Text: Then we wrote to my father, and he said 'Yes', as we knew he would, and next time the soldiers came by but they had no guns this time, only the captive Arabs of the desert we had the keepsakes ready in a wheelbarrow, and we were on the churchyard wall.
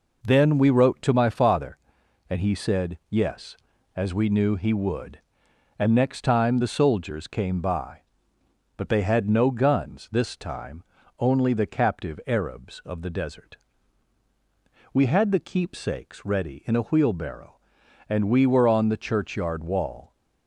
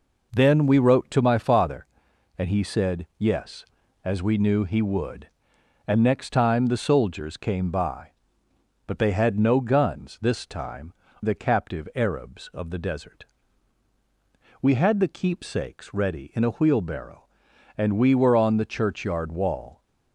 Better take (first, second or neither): first